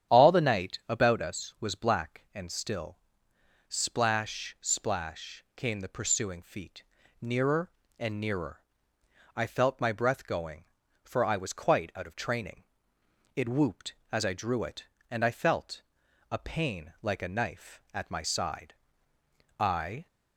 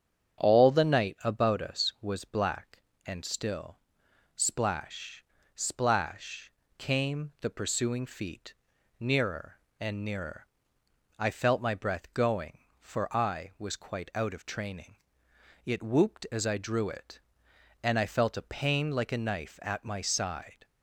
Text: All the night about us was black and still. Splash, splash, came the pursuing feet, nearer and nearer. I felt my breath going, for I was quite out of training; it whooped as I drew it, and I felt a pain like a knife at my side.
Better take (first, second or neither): second